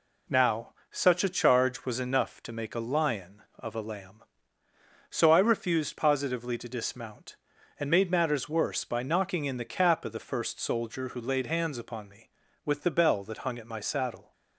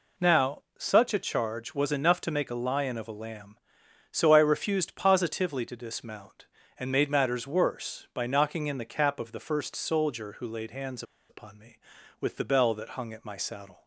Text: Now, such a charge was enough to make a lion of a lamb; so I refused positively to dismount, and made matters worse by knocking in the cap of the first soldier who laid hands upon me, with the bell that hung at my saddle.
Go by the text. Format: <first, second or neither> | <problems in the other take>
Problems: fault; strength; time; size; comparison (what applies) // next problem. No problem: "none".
first | pauses between "hands" and "upon"; slight; at 11.0 s; 0.26 s long